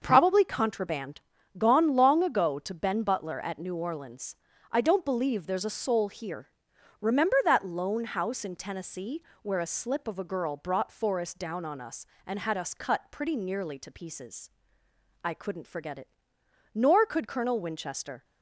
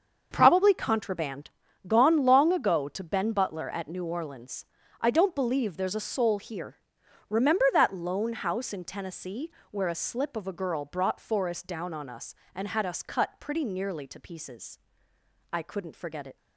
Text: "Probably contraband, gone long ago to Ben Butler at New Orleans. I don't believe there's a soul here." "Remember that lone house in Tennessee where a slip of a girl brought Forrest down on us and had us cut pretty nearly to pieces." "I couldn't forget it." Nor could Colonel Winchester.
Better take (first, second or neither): first